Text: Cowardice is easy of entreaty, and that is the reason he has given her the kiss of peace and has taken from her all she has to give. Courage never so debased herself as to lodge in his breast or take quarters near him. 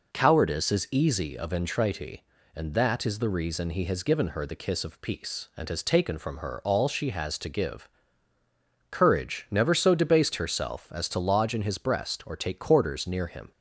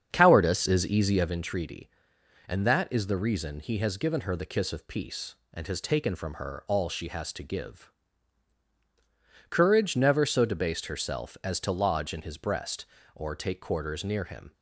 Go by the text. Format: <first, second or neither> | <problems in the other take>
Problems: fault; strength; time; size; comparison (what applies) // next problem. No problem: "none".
first | starts louder than the rest; strong; until 1.4 s; 7.5 dB